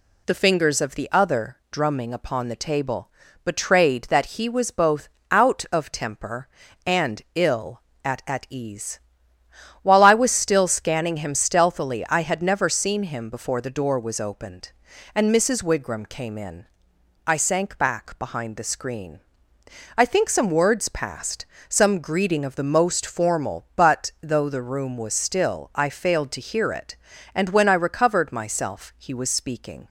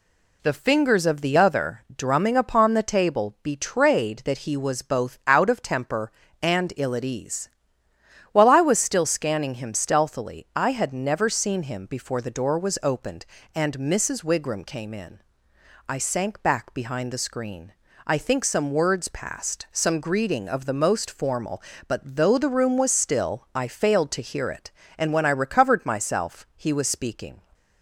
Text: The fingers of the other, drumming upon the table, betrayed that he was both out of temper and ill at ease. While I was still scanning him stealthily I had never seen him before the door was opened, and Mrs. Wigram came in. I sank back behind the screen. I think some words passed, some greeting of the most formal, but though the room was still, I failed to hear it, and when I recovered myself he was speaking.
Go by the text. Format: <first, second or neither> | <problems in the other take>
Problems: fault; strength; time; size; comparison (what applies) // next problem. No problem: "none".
second | pauses between "both" and "out"; slight; at 5.0 s; 0.22 s long // says "at" twice; at 8.2 s